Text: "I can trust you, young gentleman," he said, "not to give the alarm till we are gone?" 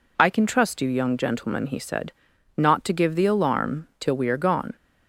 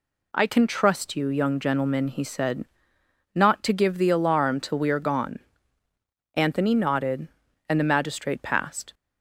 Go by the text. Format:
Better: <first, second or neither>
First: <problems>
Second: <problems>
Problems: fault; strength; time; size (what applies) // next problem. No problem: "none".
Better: first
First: none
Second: goes on to say "Anthony nodded and the magistrate passed"; strong; from 6.3 s on; 2.5 s long